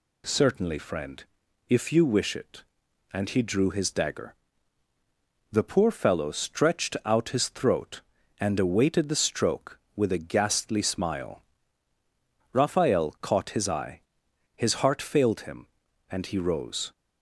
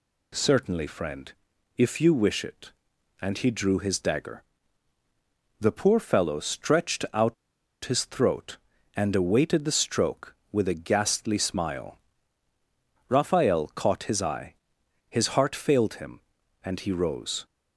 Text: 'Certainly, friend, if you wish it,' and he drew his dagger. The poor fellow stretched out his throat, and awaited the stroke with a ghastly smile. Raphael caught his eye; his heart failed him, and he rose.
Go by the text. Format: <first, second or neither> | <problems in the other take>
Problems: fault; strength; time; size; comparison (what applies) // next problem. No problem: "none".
first | pauses between "out" and "his"; noticeable; at 7.3 s; 0.50 s long